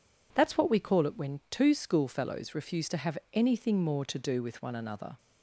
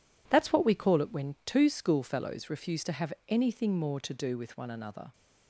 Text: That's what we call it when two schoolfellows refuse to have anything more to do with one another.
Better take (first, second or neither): first